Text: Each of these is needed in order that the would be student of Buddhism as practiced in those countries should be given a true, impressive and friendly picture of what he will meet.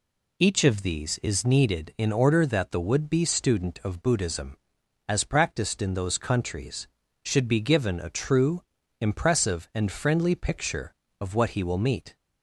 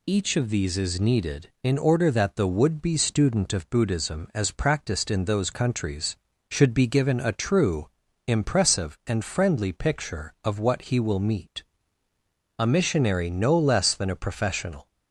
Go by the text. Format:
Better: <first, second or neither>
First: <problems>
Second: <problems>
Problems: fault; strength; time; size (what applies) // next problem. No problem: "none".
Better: first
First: none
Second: goes on to say "A missionary no less than a professional"; strong; from 12.5 s on; 2.3 s long